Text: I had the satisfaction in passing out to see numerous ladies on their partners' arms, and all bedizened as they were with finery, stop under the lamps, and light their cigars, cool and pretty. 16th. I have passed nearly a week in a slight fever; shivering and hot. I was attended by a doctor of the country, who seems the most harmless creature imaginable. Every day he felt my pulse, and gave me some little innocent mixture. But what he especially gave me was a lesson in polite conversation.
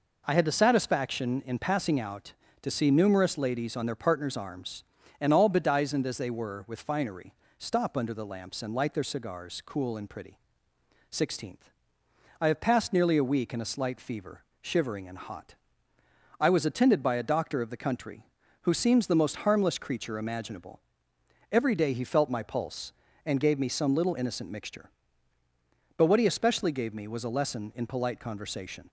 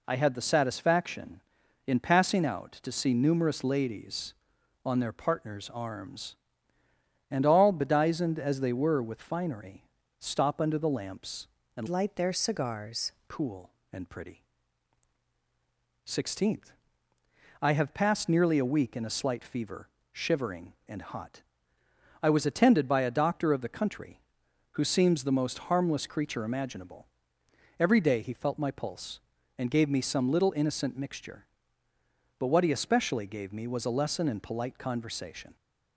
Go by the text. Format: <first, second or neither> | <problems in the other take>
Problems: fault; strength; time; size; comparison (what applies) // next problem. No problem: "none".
first | changes voice from "light" to "cigars"; from 11.8 to 13.0 s; 1.2 s long